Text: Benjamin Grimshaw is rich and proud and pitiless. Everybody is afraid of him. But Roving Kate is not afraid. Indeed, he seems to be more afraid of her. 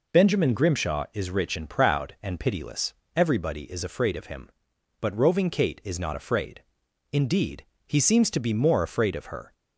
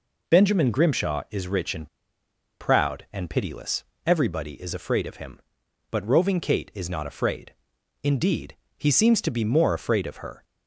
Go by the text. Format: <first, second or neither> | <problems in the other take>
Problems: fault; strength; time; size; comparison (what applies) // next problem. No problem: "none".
first | pauses between "and" and "proud"; noticeable; at 1.8 s; 0.72 s long